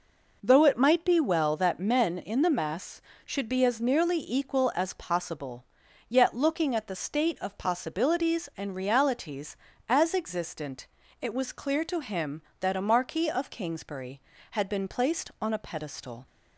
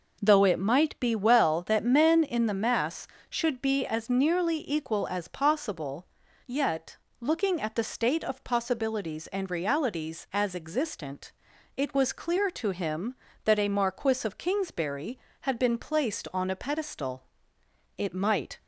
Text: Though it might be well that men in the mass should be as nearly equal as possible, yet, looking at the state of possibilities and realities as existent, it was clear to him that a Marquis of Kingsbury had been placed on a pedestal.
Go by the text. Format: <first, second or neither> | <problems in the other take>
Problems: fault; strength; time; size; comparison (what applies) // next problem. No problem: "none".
first | goes on to say "It might"; noticeable; from 17.9 s on; 0.62 s long